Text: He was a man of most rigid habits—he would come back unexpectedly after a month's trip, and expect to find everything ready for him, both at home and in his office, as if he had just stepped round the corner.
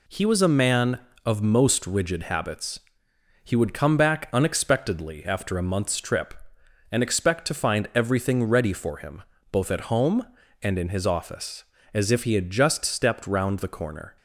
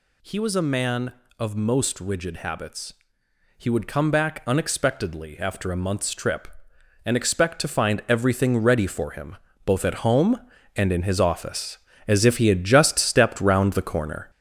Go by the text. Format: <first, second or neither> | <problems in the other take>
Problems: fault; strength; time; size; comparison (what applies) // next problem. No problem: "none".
first | gets louder; throughout; 6.5 dB